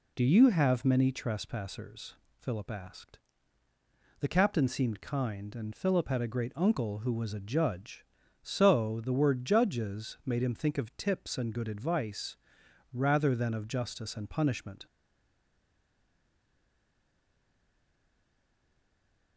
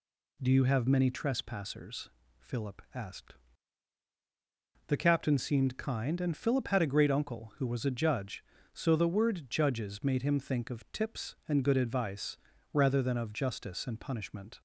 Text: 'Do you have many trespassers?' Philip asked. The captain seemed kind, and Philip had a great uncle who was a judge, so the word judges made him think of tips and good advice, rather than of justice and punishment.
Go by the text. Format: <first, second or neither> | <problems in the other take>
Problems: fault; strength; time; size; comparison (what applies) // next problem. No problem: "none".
second | stays silent after the last word; strong; from 14.8 s on; 4.5 s long